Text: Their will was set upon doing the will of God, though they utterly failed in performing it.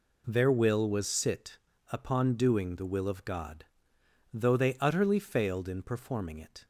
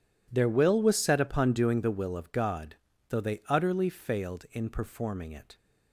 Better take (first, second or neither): second